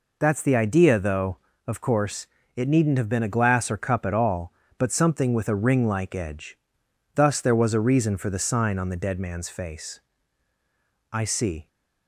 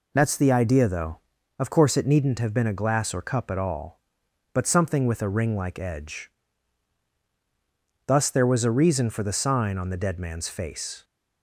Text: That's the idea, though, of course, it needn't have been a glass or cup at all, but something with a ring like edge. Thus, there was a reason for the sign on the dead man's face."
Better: second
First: goes on to say "I see"; from 11.1 s on; 0.56 s long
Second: none

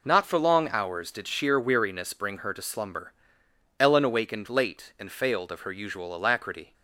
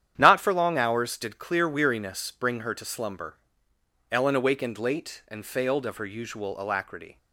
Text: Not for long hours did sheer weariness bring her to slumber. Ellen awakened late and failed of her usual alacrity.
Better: first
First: none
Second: starts louder than the rest; strong; until 1.1 s; 10 dB // says "clear" for "sheer"; at 1.3 s

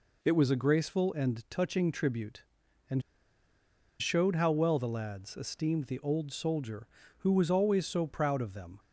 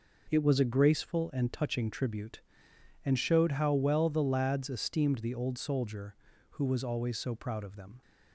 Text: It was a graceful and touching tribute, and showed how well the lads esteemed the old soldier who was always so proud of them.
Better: second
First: pauses between "and" and "showed"; at 3.0 s; 0.99 s long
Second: none

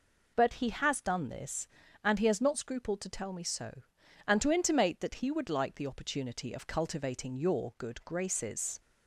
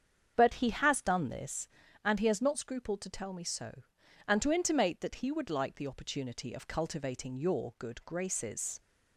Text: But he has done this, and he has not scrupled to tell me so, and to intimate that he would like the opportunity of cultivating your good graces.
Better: first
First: none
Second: starts louder than the rest; strong; until 1.6 s; 7.5 dB

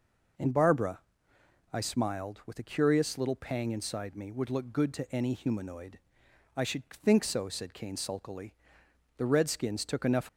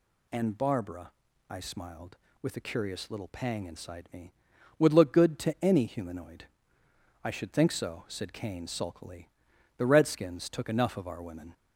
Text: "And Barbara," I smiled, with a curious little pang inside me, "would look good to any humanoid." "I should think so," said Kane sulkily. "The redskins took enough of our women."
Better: second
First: stops before "of our women"; at 10.2 s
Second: none

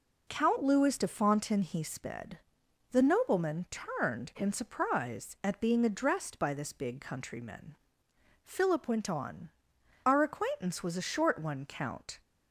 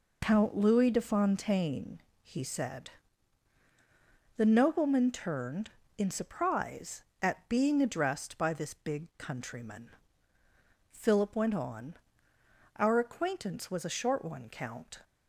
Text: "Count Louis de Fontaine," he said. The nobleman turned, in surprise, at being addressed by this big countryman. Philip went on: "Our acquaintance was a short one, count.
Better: second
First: says "sped" for "said"; at 1.8 s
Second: none

